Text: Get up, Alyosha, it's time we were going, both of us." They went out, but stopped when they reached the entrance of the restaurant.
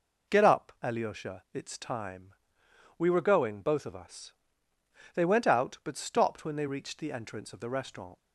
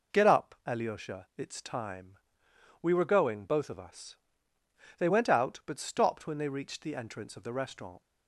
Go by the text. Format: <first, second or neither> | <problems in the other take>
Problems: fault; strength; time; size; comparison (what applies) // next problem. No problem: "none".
neither | pauses between "time" and "we"; noticeable; the same in both